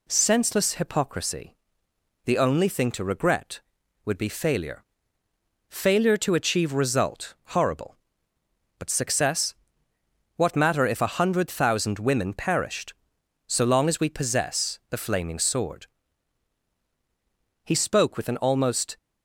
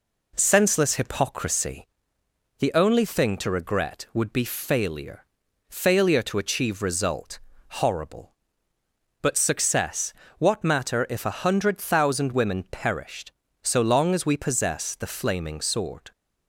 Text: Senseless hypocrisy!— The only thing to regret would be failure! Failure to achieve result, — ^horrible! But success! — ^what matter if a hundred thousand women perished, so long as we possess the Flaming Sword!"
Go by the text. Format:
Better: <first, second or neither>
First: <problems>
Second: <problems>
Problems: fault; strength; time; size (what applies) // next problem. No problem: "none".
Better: second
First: goes on to say "He spoke with an almost"; from 17.6 s on; 1.3 s long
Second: none